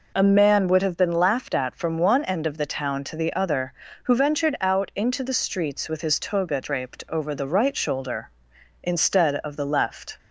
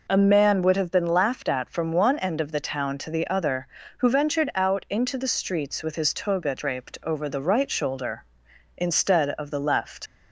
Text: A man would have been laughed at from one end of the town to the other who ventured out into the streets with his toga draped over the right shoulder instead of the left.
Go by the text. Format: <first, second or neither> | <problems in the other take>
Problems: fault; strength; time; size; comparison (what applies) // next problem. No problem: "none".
first | leaves "left" unfinished; at 10.0 s; 65 ms